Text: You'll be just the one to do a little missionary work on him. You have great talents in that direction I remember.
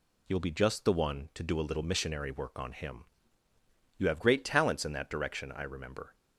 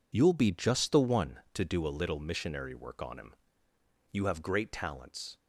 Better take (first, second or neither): first